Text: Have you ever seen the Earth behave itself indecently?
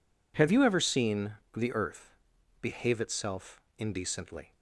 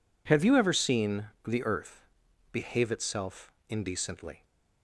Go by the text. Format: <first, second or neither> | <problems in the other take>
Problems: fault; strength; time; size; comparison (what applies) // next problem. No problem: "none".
neither | pauses between "seen" and "the"; slight; the same in both // pauses between "Earth" and "behave"; the same in both // pauses between "itself" and "indecently"; slight; the same in both